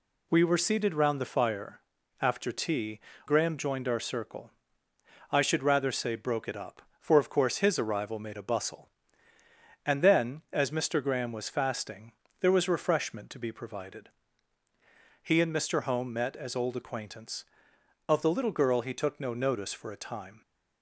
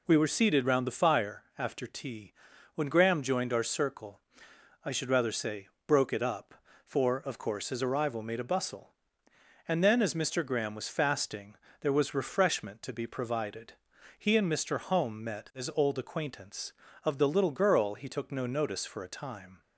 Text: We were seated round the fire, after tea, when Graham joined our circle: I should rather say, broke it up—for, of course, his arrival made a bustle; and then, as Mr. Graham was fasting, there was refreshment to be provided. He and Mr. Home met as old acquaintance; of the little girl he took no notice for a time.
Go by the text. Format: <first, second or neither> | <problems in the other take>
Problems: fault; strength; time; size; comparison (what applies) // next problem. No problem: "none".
second | skips "when"; at 3.1 s